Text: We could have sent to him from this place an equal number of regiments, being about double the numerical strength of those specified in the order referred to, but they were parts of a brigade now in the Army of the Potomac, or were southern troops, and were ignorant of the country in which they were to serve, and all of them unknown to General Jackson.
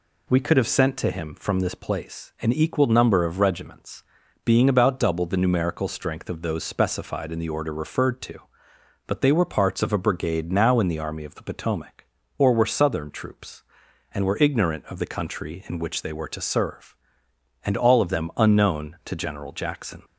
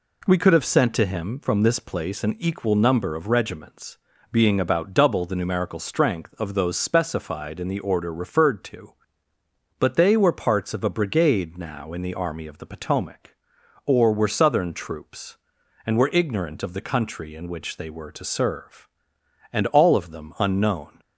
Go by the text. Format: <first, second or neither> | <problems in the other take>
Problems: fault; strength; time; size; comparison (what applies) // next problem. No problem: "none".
first | stops before "to General Jackson"; at 20.9 s